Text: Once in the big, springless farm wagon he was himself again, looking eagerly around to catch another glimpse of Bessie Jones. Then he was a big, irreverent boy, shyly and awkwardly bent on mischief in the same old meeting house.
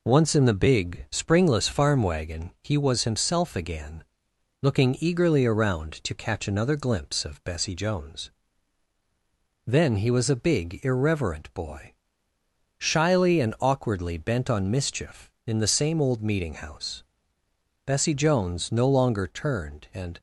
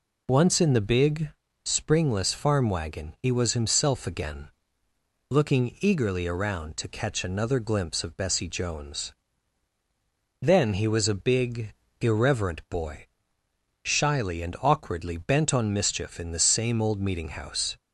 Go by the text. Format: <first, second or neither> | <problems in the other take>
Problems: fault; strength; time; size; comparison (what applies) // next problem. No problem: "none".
second | goes on to say "Bessie Jones no longer turned and"; strong; from 17.8 s on; 2.3 s long